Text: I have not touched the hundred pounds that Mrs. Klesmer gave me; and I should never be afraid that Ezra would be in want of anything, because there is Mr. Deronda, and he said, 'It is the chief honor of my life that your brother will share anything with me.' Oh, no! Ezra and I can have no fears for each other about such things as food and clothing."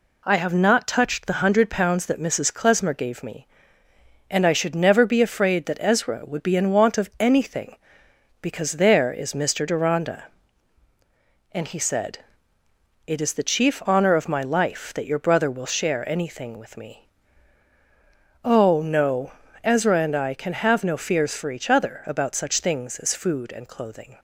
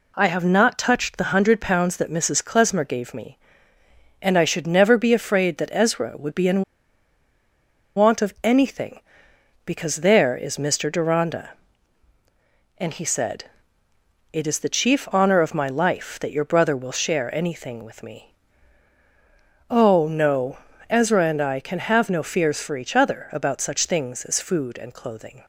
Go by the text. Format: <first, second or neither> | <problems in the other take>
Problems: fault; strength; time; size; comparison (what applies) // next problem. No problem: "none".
first | pauses between "in" and "want"; strong; at 6.6 s; 1.3 s long